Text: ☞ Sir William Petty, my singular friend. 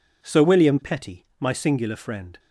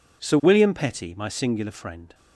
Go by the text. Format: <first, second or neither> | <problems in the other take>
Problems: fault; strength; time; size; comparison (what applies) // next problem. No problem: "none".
neither | none